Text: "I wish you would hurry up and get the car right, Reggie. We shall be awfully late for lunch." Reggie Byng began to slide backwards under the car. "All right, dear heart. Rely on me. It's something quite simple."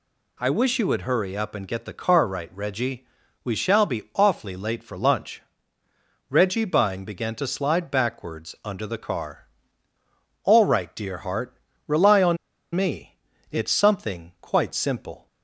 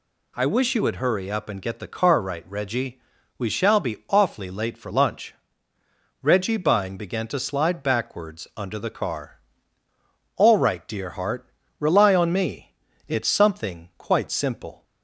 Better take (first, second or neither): second